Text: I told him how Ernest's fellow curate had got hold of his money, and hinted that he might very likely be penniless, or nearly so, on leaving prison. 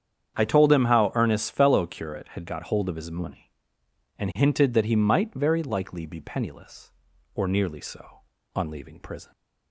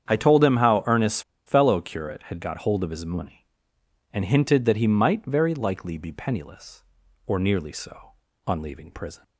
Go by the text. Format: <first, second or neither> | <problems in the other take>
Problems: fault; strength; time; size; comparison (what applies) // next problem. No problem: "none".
first | starts louder than the rest; strong; until 1.1 s; 8.5 dB; strong in the first // pauses between "Ernest's" and "fellow"; slight; at 1.2 s; 0.24 s long